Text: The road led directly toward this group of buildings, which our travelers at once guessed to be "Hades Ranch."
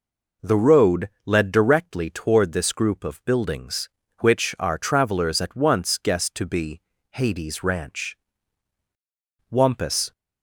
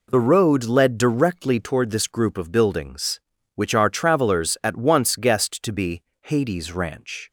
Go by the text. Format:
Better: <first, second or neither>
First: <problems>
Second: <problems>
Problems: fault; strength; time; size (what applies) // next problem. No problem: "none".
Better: second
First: pauses between "road" and "led"; slight; at 1.0 s; 0.16 s long // pauses between "be" and "Hades"; slight; at 6.7 s; 0.32 s long // goes on to say "Wampus"; noticeable; from 9.4 s on; 0.62 s long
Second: pauses between "be" and "Hades"; slight; at 6.0 s; 0.22 s long